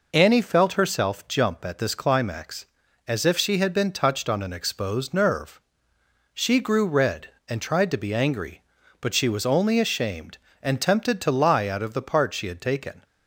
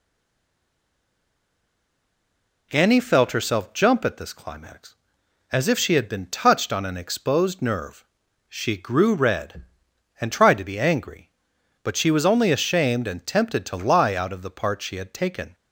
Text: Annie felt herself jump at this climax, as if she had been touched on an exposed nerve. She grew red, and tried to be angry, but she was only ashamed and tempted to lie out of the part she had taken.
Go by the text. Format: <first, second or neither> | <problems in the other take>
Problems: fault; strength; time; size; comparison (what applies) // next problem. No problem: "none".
first | stays silent before the first word; strong; until 2.7 s; 2.7 s long